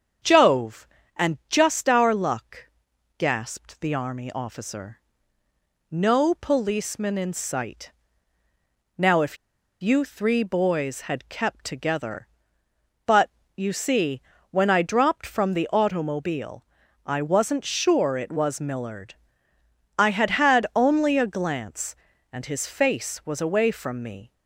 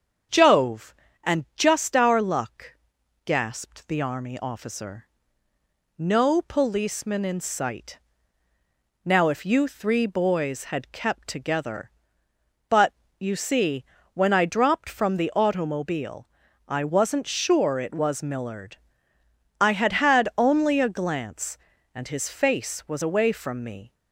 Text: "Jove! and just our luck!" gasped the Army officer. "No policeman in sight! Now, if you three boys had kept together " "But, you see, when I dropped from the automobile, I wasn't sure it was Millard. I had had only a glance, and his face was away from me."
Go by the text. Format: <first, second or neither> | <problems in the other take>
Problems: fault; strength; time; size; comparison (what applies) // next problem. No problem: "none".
second | starts louder than the rest; strong; until 1.6 s; 7.5 dB; strong in the second // pauses between "if" and "you"; at 9.3 s; 0.44 s long